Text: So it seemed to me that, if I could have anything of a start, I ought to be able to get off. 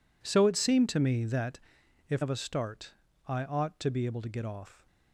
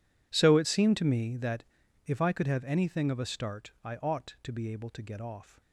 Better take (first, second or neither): second